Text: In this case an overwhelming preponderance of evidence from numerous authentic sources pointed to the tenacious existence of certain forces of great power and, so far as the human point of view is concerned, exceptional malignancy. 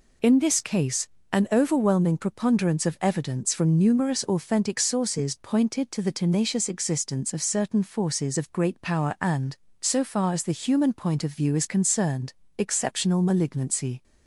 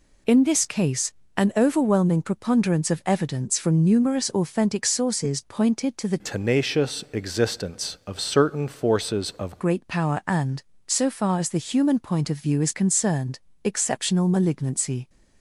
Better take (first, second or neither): first